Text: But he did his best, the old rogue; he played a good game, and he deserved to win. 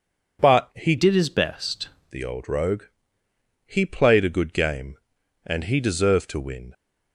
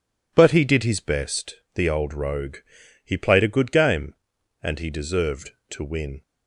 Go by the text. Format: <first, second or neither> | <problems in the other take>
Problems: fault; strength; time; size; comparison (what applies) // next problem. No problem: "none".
second | changes voice from "did" to "best"; from 0.9 to 1.8 s; 0.9 s long